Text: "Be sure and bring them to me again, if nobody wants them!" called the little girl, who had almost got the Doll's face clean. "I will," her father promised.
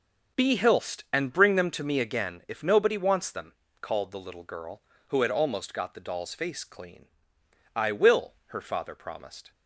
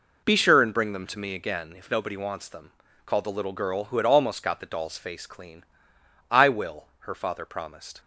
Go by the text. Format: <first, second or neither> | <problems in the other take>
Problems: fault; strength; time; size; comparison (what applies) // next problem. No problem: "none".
second | says "hilst" for "sure"; at 0.5 s